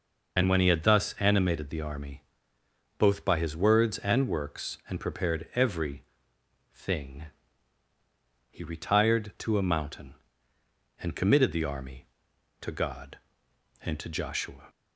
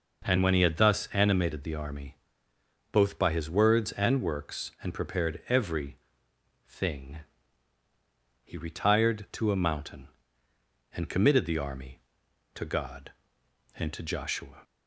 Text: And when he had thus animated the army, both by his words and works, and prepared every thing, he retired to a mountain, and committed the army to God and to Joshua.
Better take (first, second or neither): second